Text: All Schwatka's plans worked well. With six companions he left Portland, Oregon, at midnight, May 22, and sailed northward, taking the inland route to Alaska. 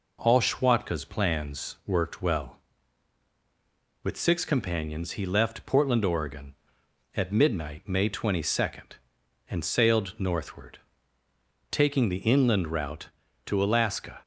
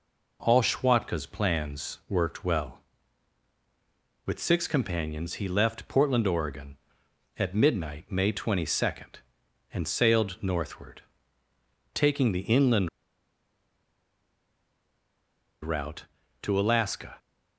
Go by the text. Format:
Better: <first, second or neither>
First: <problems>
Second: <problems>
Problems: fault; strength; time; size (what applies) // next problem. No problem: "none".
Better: first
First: none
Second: pauses between "inland" and "route"; strong; at 12.8 s; 2.7 s long